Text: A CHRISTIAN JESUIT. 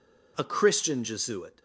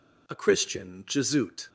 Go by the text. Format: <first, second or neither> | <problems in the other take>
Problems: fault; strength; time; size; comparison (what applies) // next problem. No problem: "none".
neither | none